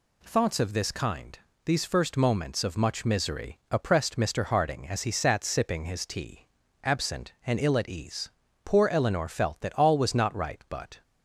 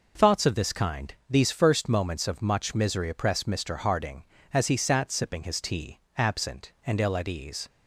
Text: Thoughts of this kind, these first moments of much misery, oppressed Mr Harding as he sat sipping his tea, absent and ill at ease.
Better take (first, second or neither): second